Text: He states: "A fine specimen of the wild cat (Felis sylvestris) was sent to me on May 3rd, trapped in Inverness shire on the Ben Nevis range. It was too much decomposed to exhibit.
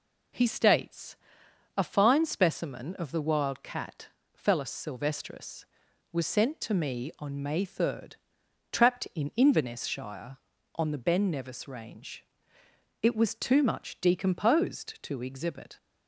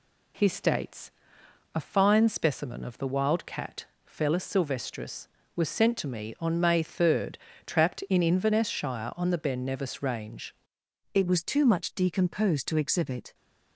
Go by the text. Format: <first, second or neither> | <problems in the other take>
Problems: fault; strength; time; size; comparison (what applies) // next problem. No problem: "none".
first | changes voice at "It"; from 11.1 s on; 2.2 s long